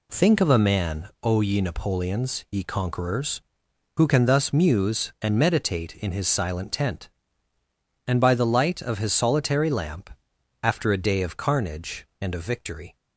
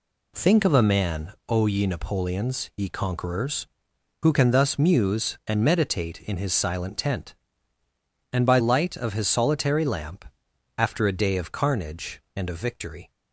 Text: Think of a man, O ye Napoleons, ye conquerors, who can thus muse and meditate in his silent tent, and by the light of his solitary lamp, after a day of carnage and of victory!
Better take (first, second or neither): first